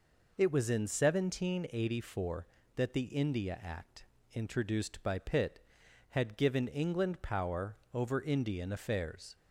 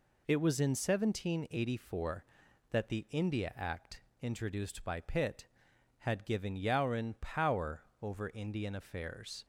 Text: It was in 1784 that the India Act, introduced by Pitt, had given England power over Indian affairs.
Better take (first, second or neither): first